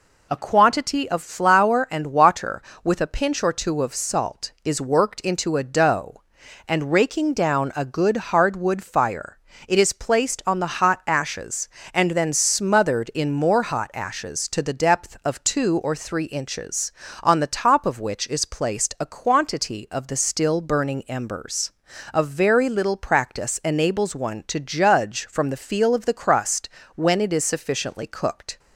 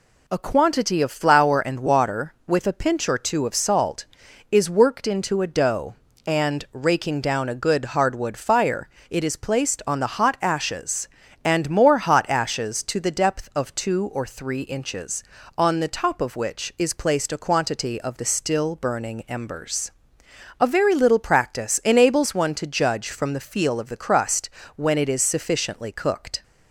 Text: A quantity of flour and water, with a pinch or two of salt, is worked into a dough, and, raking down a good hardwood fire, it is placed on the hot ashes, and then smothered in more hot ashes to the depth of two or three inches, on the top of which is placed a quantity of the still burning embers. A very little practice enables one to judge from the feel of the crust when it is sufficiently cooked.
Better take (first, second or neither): first